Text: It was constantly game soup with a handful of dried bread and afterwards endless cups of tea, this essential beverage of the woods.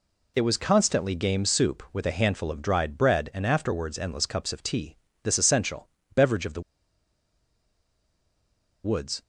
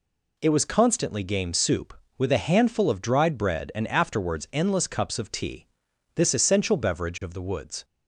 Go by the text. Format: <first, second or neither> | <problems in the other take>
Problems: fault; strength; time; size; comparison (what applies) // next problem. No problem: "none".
second | pauses between "essential" and "beverage"; slight; at 5.8 s; 0.28 s long // pauses between "the" and "woods"; strong; at 6.6 s; 2.2 s long